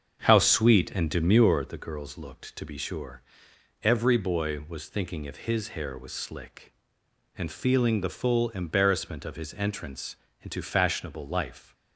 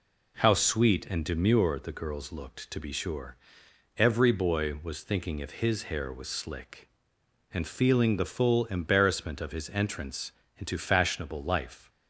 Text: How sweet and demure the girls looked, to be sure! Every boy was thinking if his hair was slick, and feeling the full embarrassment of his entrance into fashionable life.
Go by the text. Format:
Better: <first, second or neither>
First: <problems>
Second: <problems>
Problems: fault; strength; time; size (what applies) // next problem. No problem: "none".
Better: second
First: starts louder than the rest; until 1.7 s; 7 dB // pauses between "entrance" and "into"; slight; at 10.1 s; 0.26 s long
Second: pauses between "entrance" and "into"; slight; at 10.3 s; 0.26 s long